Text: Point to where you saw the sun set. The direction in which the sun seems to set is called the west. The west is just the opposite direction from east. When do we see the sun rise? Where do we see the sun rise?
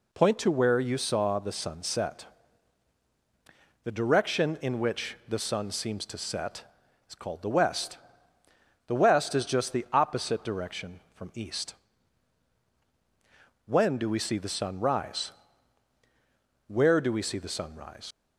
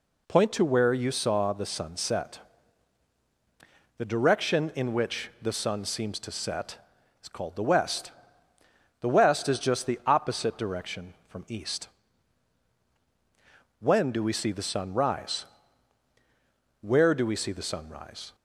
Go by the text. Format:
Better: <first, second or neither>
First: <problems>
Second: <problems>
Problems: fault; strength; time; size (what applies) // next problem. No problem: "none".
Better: second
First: leaves "rise" unfinished; at 18.1 s; 105 ms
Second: none